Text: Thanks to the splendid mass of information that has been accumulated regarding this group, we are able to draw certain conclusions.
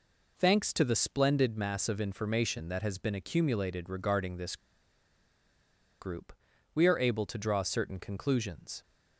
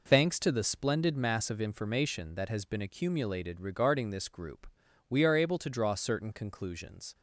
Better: second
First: pauses between "this" and "group"; strong; at 4.5 s; 1.4 s long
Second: none

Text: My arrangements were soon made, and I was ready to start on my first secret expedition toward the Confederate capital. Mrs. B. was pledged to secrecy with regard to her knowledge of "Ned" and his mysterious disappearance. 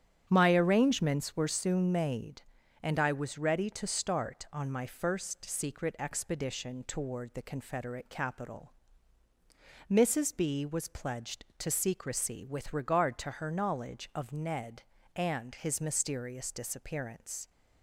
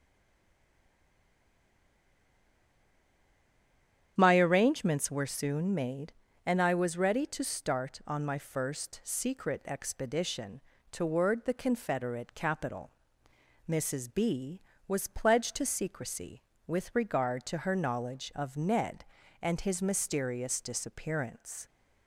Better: first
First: starts louder than the rest; strong; until 1.2 s; 9 dB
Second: stays silent before the first word; strong; until 4.1 s; 4.1 s long // starts louder than the rest; strong; until 5.1 s; 9 dB // pauses between "expedition" and "toward"; slight; at 10.6 s; 0.28 s long

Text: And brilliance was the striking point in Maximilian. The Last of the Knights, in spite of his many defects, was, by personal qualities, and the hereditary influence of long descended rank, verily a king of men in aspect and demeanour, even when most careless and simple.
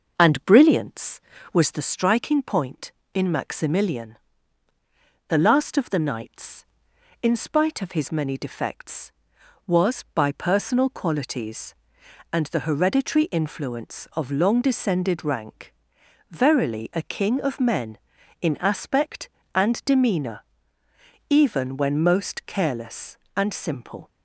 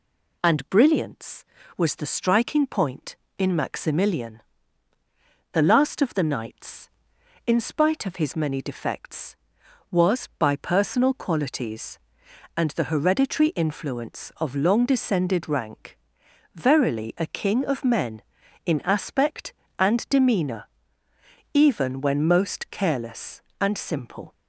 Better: second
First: starts louder than the rest; noticeable; until 1.9 s; 6 dB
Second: none

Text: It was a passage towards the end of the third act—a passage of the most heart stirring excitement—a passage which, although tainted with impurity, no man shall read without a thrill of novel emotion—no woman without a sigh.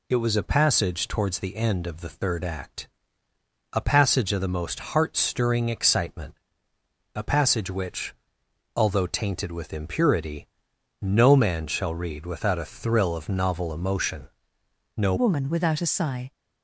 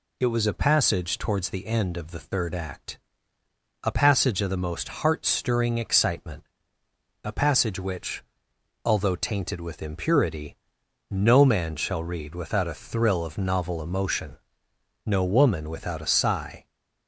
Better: second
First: changes voice at "woman"; from 15.1 s on; 1.2 s long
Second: none

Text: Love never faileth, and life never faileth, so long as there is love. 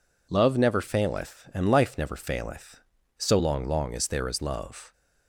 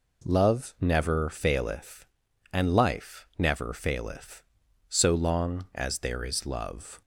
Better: second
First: says "long" twice; at 3.6 s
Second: none

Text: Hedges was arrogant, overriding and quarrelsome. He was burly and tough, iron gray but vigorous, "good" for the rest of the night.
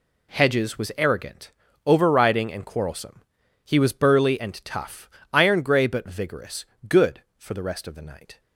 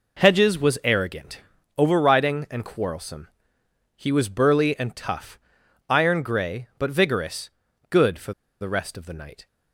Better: first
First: none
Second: pauses between "for" and "the"; slight; at 8.3 s; 0.29 s long

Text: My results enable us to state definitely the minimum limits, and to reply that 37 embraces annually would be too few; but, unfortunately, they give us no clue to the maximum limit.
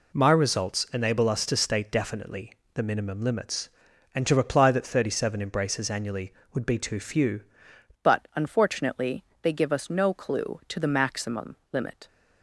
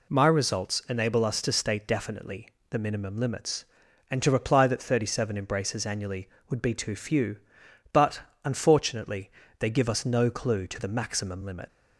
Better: second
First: pauses between "definitely" and "the"; slight; at 2.5 s; 0.22 s long // changes voice at "but"; from 8.0 s on; 4.0 s long // pauses between "maximum" and "limit"; slight; at 11.5 s; 0.16 s long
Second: pauses between "definitely" and "the"; slight; at 2.4 s; 0.22 s long

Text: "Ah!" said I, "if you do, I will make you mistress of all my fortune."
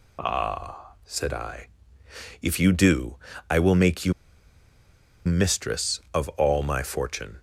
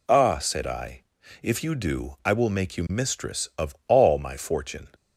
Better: second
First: pauses between "you" and "mistress"; at 4.1 s; 1.1 s long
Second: none

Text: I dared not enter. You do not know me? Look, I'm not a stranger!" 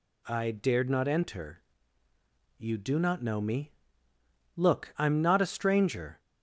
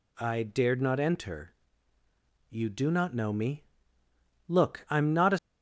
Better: first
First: none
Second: stops before "stranger"; at 5.3 s

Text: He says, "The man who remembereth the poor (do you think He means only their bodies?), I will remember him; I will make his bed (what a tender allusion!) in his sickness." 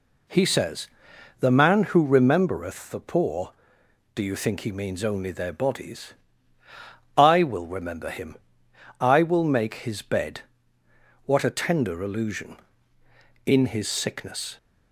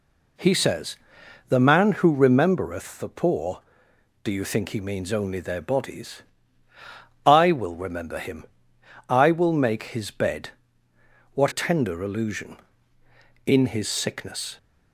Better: first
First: none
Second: skips "a"; at 11.5 s

